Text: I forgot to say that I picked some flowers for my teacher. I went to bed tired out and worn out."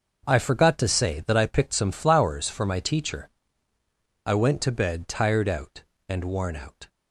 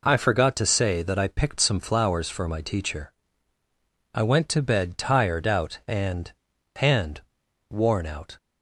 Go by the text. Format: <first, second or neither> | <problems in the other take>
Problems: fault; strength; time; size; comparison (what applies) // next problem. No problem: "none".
first | says "and" twice; at 6.7 s